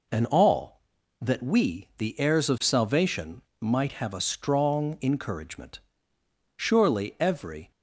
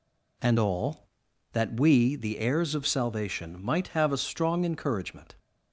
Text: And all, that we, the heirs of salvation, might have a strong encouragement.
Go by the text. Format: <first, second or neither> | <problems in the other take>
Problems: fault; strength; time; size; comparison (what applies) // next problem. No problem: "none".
second | goes on to say "Surely every"; noticeable; from 6.5 s on; 1.1 s long